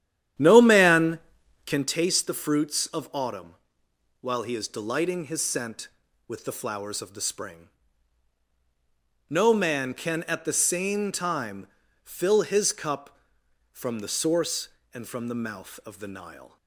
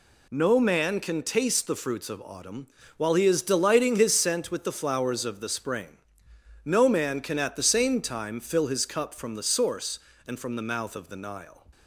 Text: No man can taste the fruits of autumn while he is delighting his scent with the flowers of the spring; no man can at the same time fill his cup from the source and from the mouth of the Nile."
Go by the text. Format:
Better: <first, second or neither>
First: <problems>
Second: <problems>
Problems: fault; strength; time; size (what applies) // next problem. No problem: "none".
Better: second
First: starts louder than the rest; strong; until 1.9 s; 10.5 dB // pauses between "autumn" and "while"; noticeable; at 3.5 s; 0.66 s long // pauses between "time" and "fill"; slight; at 11.6 s; 0.34 s long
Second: pauses between "autumn" and "while"; slight; at 2.6 s; 0.32 s long